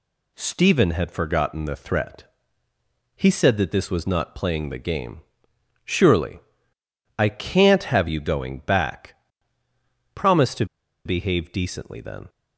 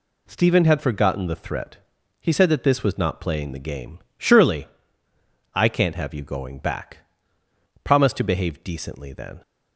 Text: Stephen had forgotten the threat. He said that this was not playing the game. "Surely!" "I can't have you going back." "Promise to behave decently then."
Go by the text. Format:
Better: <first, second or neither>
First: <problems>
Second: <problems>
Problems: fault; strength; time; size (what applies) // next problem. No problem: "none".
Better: second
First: pauses between "to" and "behave"; at 10.6 s; 0.40 s long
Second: none